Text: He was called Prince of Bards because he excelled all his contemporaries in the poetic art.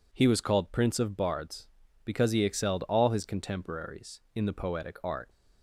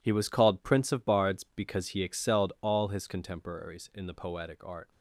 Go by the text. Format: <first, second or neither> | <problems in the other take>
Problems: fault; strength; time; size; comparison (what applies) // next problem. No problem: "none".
first | gets quieter; strong; throughout; 11 dB